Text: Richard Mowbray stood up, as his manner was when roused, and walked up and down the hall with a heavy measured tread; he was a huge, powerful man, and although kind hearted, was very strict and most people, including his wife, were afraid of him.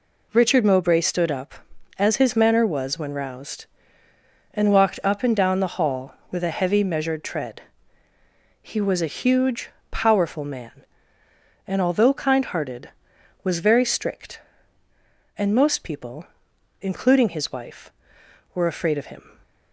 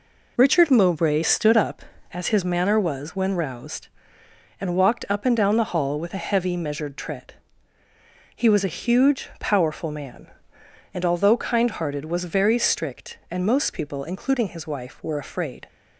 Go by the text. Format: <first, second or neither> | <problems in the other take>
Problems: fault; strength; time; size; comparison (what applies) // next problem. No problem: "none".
first | stops before "of him"; at 15.6 s